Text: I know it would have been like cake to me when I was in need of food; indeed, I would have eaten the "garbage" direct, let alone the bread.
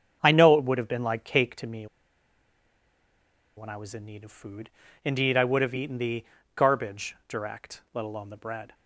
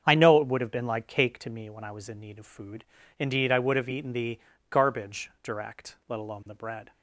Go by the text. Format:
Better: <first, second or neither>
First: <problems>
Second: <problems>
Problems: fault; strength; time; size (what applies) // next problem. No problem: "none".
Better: second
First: starts louder than the rest; strong; until 1.2 s; 7.5 dB // pauses between "me" and "when"; strong; at 1.8 s; 1.6 s long // pauses between "the" and "garbage"; slight; at 6.2 s; 0.28 s long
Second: starts louder than the rest; strong; until 1.0 s; 7.5 dB // pauses between "the" and "garbage"; slight; at 4.4 s; 0.28 s long